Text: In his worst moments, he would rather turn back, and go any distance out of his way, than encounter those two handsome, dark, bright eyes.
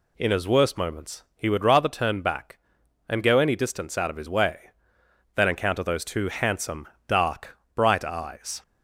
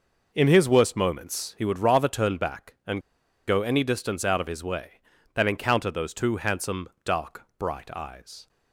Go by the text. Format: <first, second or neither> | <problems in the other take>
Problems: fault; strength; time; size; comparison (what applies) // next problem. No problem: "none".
first | pauses between "and" and "go"; noticeable; at 3.0 s; 0.46 s long